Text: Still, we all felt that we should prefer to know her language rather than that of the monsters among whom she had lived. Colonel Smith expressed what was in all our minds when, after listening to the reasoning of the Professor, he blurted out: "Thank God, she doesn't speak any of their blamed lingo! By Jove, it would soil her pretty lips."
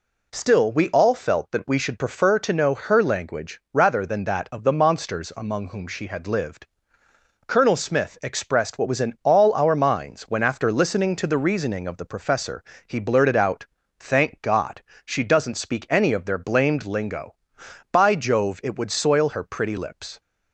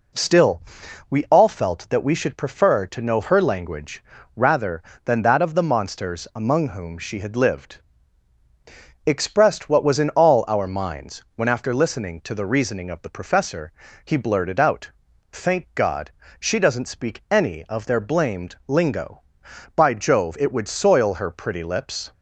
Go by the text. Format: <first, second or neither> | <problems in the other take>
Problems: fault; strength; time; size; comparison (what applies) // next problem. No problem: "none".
first | pauses between "language" and "rather"; slight; at 4.0 s; 0.32 s long // skips "Colonel Smith"; at 8.4 s